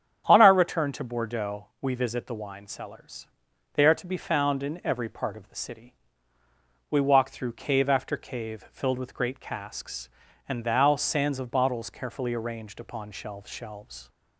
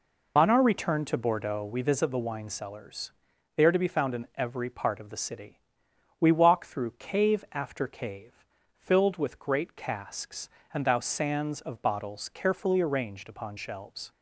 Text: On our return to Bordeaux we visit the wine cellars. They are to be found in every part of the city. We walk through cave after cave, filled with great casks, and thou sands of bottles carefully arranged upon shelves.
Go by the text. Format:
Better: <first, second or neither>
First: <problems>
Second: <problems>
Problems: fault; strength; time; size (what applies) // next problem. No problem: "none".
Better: second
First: starts louder than the rest; strong; until 1.2 s; 9 dB // pauses between "Bordeaux" and "we"; slight; at 1.6 s; 0.16 s long // says "shelves" twice; at 13.5 s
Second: none